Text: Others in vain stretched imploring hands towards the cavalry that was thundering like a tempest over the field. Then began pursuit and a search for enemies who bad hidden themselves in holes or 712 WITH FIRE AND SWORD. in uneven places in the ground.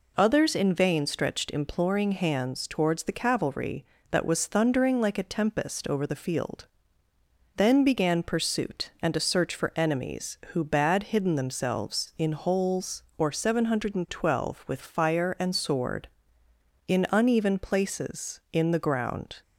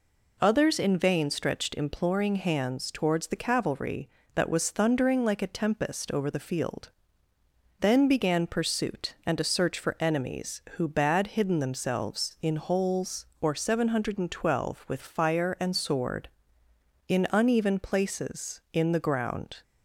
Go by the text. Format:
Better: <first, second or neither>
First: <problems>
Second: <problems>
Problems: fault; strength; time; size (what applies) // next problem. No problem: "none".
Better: neither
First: none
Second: none